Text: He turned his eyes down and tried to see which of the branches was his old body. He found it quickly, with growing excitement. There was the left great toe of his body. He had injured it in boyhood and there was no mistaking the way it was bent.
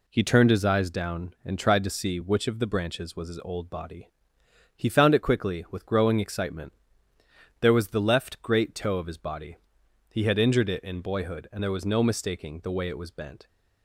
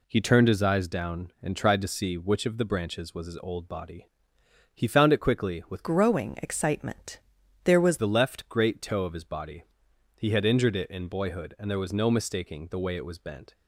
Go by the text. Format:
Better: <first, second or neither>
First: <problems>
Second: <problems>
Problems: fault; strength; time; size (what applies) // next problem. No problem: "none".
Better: first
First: none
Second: changes voice from "growing" to "was"; from 5.8 to 7.9 s; 2.1 s long